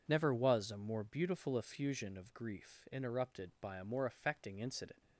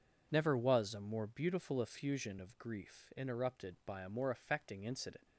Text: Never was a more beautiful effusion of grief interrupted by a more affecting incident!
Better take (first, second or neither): neither